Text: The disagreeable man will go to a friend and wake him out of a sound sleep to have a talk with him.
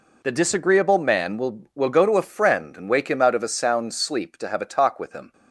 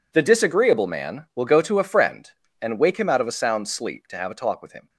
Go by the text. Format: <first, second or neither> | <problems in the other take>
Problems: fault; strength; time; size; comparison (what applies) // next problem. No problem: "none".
second | says "will" twice; at 1.7 s